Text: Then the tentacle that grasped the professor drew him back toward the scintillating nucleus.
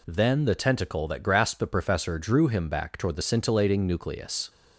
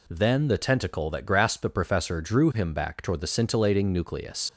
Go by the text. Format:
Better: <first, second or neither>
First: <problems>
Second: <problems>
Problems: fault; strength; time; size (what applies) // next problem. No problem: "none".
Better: first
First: none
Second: leaves "nucleus" unfinished; at 4.4 s; 65 ms